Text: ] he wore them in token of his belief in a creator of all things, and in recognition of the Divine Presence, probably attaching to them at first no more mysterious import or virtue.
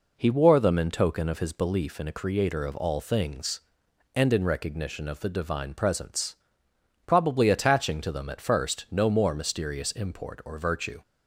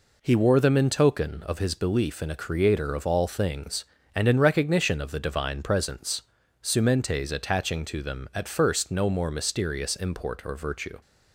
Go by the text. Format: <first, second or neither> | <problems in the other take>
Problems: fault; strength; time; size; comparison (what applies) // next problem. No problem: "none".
first | says "sumentes" for "probably"; at 6.6 s